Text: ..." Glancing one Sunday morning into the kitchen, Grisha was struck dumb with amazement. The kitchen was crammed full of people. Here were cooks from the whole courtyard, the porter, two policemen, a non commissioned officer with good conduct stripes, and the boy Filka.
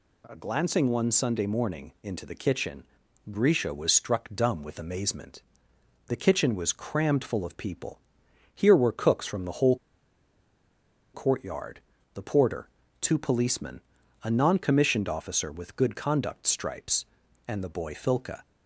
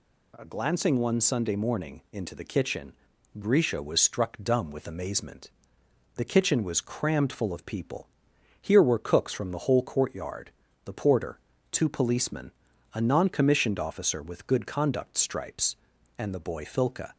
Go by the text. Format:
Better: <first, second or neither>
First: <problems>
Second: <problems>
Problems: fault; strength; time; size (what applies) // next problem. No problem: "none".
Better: second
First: pauses between "whole" and "courtyard"; strong; at 9.7 s; 1.3 s long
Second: none